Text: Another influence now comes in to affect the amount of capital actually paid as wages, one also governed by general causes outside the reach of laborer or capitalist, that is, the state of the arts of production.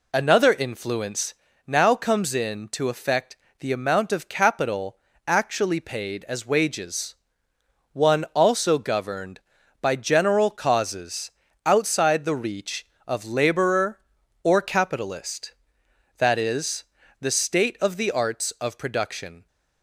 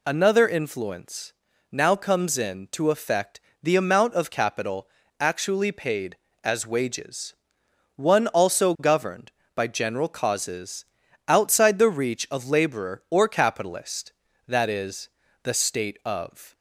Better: first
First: pauses between "influence" and "now"; slight; at 1.3 s; 0.32 s long // pauses between "affect" and "the"; slight; at 3.3 s; 0.24 s long // pauses between "capital" and "actually"; slight; at 4.9 s; 0.30 s long // pauses between "causes" and "outside"; slight; at 11.2 s; 0.36 s long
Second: pauses between "influence" and "now"; at 1.3 s; 0.38 s long // pauses between "affect" and "the"; slight; at 3.3 s; 0.24 s long // pauses between "capital" and "actually"; slight; at 4.8 s; 0.32 s long // pauses between "causes" and "outside"; at 10.8 s; 0.42 s long // stops before "the arts of production"; at 16.5 s

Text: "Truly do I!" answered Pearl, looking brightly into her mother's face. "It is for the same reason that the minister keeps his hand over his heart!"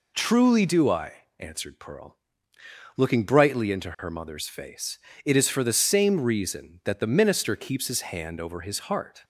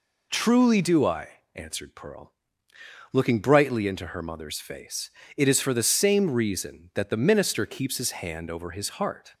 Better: neither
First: none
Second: none

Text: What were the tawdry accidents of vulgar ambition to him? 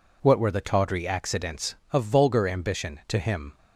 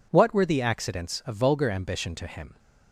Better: first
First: none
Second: skips "tawdry"; at 0.6 s

